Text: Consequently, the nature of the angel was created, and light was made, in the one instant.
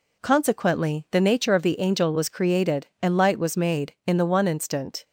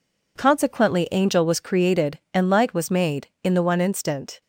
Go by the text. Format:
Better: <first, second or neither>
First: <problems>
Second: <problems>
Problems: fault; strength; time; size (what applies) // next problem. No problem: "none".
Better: first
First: none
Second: skips "the nature of the"; at 1.1 s